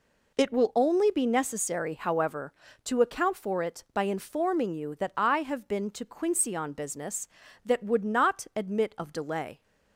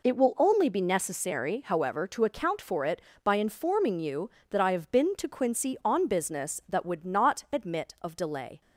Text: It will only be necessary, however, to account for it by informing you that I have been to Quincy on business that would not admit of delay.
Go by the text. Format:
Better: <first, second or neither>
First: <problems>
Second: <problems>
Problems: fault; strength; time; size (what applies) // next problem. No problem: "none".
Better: neither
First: none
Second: none